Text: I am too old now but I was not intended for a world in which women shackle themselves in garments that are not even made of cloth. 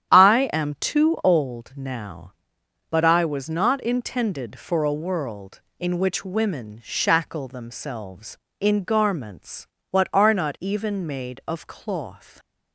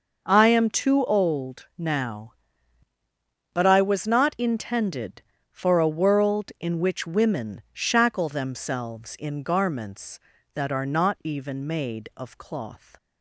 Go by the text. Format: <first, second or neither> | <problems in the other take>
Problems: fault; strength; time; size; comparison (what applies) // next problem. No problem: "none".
second | starts louder than the rest; strong; until 1.1 s; 10 dB // says "what" for "that"; at 9.9 s